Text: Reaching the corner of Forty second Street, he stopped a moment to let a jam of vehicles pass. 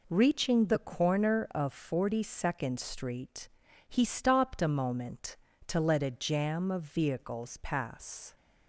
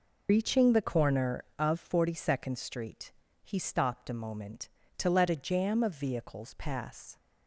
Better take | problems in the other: first | loses the start of "Reaching"; at 0.2 s; 105 ms

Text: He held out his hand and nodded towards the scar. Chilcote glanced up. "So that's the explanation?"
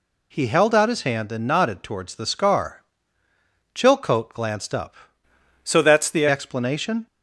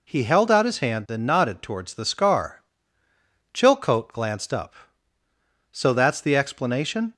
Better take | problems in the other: second | changes voice from "So" to "the"; from 5.6 to 6.2 s; 0.6 s long

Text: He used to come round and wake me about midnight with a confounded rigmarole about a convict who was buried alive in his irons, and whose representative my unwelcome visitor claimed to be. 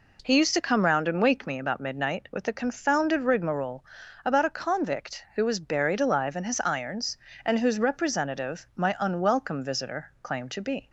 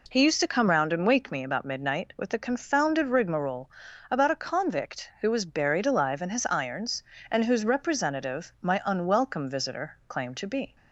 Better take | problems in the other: neither | pauses between "rigmarole" and "about"; the same in both

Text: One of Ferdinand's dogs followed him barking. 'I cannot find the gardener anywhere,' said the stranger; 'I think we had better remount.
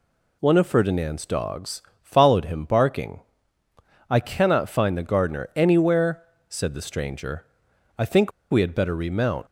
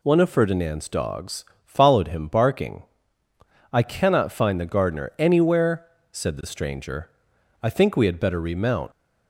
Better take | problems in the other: second | pauses between "dogs" and "followed"; slight; at 1.8 s; 0.20 s long; slight in the second // pauses between "think" and "we"; slight; at 8.3 s; 0.19 s long

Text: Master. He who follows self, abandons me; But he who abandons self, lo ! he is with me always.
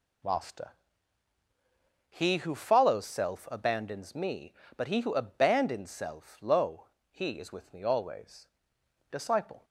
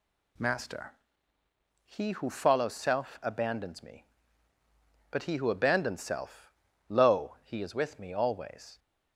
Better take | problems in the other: second | goes on to say "Disciple"; from 9.1 s on; 0.54 s long

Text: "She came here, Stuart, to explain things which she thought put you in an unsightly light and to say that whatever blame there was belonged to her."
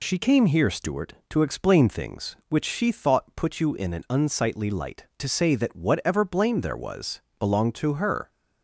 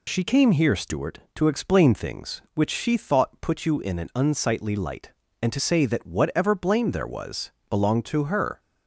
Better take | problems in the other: second | skips "and"; at 5.1 s // pauses between "was" and "belonged"; slight; at 7.1 s; 0.20 s long; slight in the second

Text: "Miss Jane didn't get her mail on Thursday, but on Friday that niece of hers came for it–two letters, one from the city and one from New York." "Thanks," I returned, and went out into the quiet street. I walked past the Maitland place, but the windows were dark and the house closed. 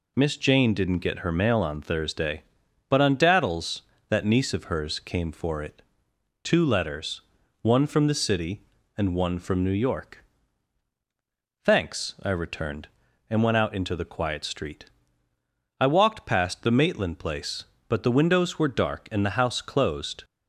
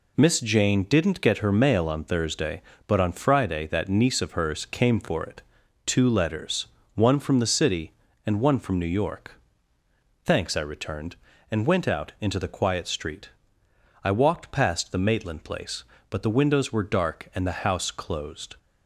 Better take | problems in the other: second | says "Daddles" for "Friday"; at 3.1 s

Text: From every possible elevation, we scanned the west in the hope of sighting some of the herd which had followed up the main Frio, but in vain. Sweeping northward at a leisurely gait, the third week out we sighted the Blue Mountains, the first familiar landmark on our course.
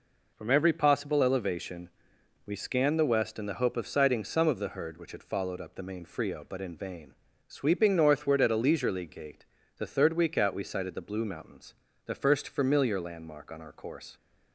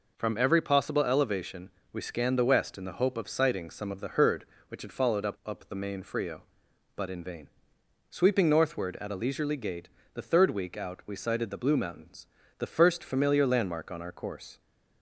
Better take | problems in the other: first | says "up" twice; at 5.4 s

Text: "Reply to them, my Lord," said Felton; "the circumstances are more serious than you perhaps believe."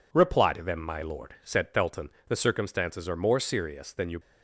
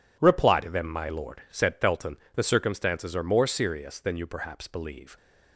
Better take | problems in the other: second | stops before "perhaps believe"; at 4.2 s

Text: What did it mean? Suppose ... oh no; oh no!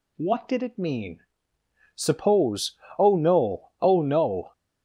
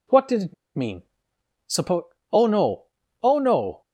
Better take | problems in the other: first | pauses between "it" and "mean"; slight; at 0.5 s; 0.22 s long

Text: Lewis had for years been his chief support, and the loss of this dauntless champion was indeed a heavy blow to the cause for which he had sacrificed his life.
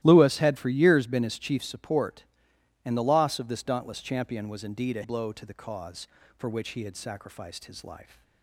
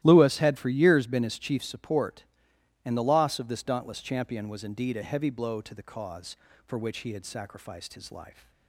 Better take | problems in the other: second | starts louder than the rest; strong; until 1.0 s; 14.5 dB; strong in the second // skips "heavy"; at 5.0 s

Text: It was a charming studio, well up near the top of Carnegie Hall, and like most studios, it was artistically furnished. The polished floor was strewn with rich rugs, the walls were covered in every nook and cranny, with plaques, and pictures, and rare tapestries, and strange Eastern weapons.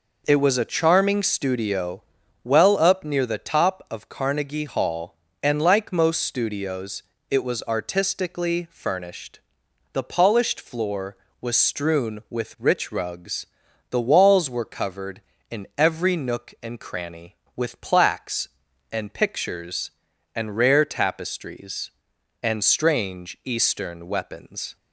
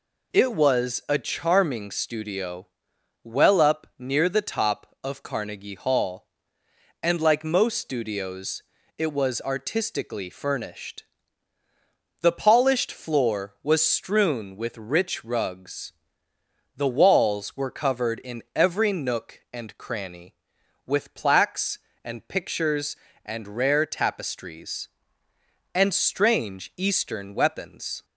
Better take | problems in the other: neither | none

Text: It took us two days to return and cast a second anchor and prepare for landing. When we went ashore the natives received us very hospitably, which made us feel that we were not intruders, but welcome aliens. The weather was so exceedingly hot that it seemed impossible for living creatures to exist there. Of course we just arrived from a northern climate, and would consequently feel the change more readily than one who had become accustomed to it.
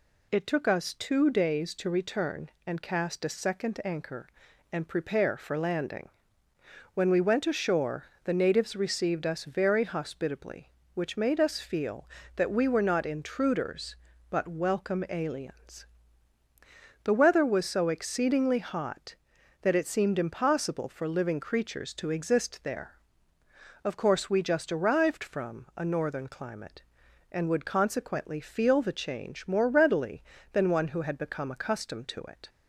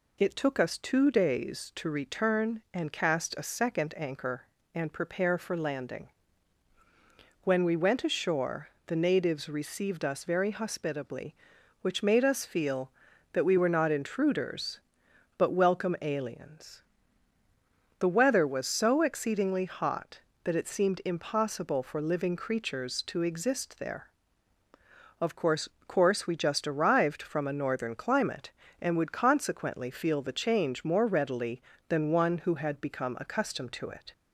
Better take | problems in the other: first | pauses between "ashore" and "the"; slight; at 8.6 s; 0.20 s long; slight in the first // says "course" twice; at 25.8 s

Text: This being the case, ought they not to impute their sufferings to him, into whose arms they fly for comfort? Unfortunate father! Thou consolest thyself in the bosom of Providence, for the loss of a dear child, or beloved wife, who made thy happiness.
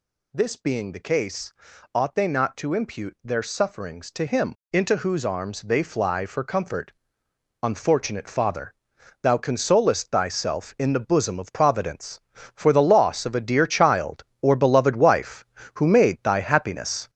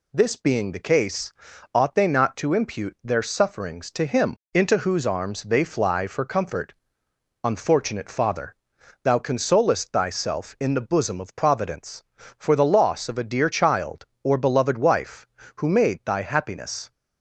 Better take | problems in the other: second | gets louder; throughout; 7 dB

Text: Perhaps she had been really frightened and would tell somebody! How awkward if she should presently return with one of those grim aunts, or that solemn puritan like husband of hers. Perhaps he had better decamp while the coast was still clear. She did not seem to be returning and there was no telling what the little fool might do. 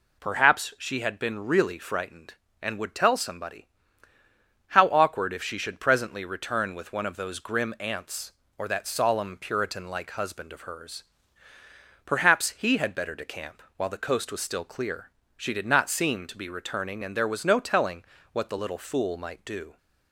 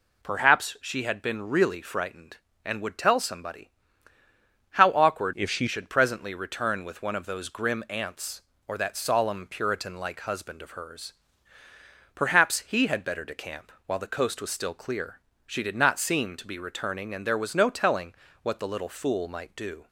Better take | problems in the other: first | changes voice from "if" to "she"; from 5.3 to 5.6 s; 0.3 s long // pauses between "telling" and "what"; slight; at 18.1 s; 0.28 s long; slight in the first

